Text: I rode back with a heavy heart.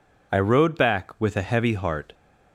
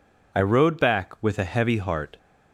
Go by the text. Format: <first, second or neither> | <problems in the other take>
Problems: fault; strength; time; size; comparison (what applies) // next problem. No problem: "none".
neither | none